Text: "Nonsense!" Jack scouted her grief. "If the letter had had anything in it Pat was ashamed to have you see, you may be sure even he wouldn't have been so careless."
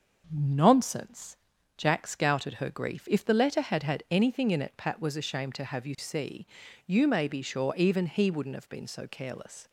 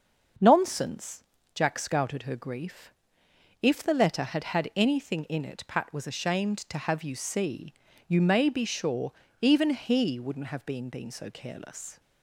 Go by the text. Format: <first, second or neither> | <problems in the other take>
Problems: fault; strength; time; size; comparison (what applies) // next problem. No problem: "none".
first | starts louder than the rest; until 1.7 s; 6.5 dB; also in the first // pauses between "sure" and "even"; slight; at 9.1 s; 0.26 s long // says "been" twice; at 10.8 s